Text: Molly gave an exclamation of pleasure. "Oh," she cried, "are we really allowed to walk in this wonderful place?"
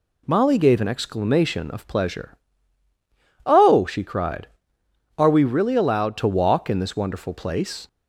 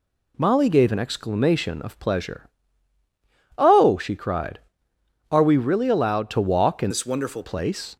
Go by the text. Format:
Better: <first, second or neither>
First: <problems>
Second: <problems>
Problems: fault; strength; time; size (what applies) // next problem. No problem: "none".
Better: first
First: none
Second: changes voice from "this" to "wonderful"; from 6.9 to 7.4 s; 0.5 s long